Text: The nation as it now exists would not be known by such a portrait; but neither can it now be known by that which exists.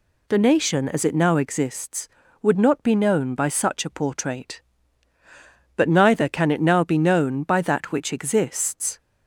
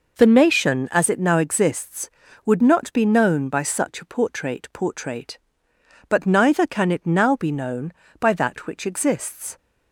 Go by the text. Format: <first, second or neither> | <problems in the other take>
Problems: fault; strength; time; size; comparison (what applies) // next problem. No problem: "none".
first | says "portrait" twice; at 4.7 s